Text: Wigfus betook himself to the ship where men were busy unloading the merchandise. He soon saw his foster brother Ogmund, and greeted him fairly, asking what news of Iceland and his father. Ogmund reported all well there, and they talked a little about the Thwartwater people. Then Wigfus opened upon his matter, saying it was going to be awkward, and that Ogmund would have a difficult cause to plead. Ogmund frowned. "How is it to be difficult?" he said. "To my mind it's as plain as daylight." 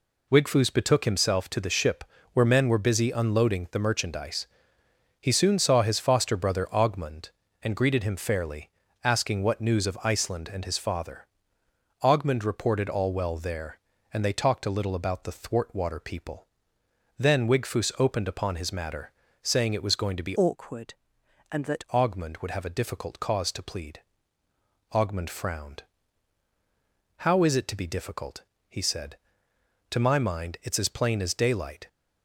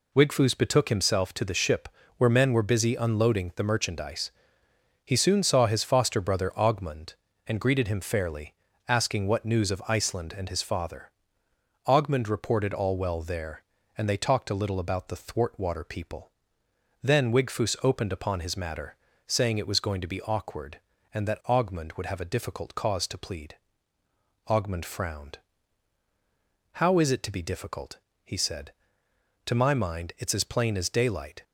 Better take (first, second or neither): second